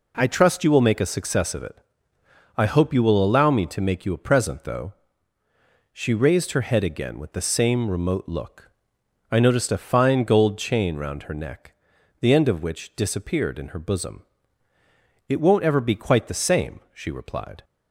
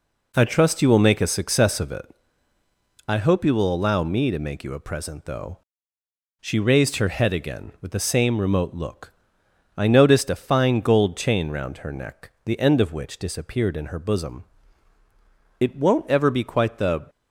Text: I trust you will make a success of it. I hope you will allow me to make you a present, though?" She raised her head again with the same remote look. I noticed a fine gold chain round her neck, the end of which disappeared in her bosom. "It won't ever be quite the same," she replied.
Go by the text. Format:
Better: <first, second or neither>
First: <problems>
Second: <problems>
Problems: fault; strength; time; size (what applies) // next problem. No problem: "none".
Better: first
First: none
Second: stops before "same she replied"; at 17.0 s